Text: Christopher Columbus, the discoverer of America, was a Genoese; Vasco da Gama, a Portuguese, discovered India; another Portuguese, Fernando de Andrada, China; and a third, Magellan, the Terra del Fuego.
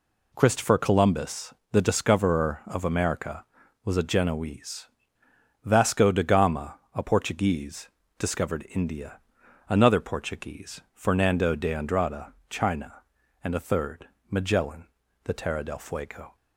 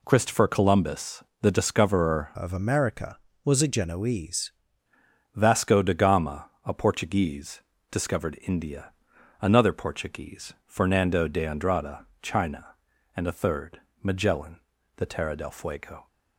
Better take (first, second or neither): first